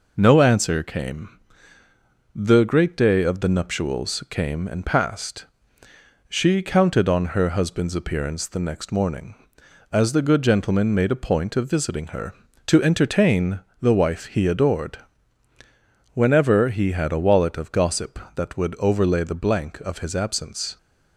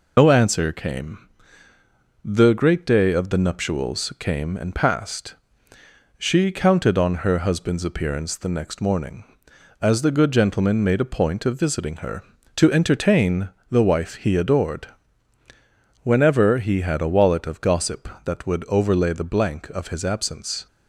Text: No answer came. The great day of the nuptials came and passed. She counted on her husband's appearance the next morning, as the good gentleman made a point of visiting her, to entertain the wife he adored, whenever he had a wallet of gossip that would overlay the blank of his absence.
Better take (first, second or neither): first